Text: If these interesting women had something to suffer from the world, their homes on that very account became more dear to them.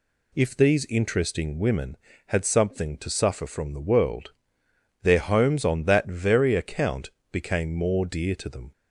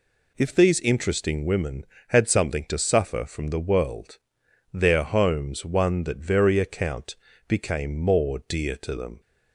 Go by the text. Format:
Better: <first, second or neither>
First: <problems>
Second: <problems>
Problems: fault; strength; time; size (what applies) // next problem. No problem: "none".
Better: first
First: pauses between "account" and "became"; slight; at 7.0 s; 0.24 s long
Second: says "one" for "on"; at 5.6 s // pauses between "account" and "became"; slight; at 7.1 s; 0.32 s long